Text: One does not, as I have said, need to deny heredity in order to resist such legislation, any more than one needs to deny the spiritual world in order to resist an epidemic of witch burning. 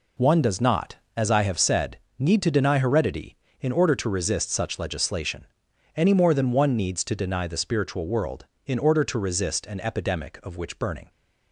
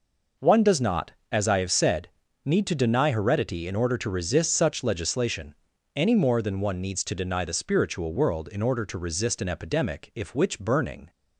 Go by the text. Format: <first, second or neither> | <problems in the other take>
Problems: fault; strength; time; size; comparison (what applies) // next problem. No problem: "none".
first | says "if" for "of"; at 10.1 s